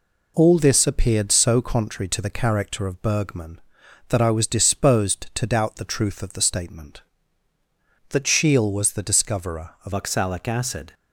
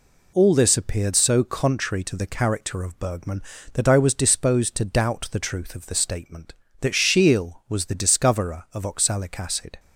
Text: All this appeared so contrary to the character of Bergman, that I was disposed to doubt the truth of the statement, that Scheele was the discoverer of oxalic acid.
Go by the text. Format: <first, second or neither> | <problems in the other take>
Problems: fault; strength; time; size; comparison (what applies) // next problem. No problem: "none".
second | changes voice at "oxalic"; from 9.9 s on; 1.0 s long